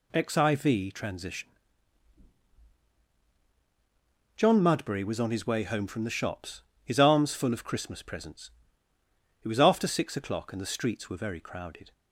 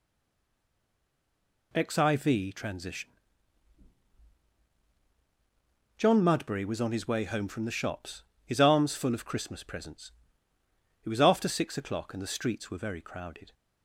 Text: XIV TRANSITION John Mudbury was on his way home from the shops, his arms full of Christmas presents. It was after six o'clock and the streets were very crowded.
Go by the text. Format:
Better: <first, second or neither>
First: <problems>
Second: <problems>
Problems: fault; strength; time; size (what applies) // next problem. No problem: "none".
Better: first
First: pauses between "TRANSITION" and "John"; strong; at 1.4 s; 2.8 s long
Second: stays silent before the first word; noticeable; until 1.7 s; 1.7 s long // pauses between "TRANSITION" and "John"; strong; at 3.0 s; 2.8 s long